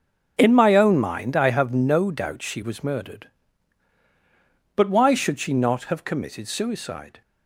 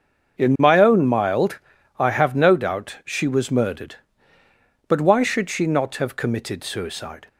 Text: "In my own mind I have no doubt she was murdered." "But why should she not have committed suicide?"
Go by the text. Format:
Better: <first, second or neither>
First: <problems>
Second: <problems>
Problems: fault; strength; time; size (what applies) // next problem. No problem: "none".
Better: first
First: starts louder than the rest; noticeable; until 1.3 s; 6 dB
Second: starts louder than the rest; until 1.4 s; 6.5 dB // says "mild" for "mind"; at 1.0 s